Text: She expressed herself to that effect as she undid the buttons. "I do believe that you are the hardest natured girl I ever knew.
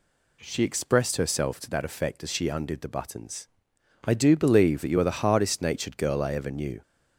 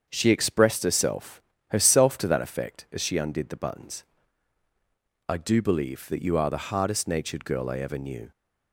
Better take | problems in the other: first | starts louder than the rest; until 1.0 s; 7 dB // says "herself" twice; at 1.7 s

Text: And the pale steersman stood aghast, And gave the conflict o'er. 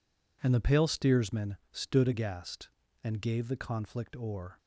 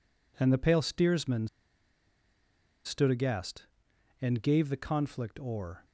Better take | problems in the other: first | pauses between "steersman" and "stood"; strong; at 1.4 s; 1.3 s long

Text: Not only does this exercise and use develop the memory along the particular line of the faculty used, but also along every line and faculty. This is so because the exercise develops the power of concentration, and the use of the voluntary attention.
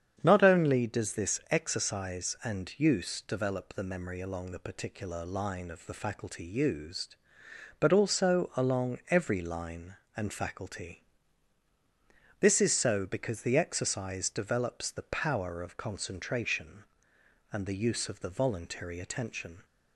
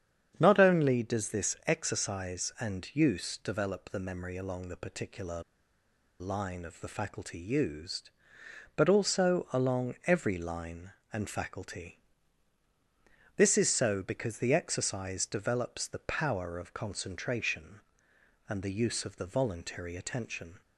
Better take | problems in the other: first | starts louder than the rest; strong; until 1.4 s; 8 dB; strong in the first // pauses between "particular" and "line"; noticeable; at 5.4 s; 0.78 s long

